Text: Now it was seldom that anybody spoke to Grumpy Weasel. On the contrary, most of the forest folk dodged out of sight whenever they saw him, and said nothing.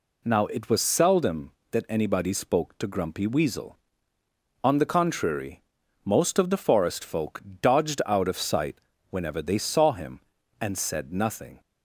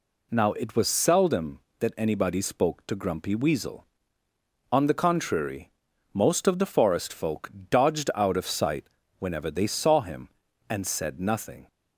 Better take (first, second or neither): neither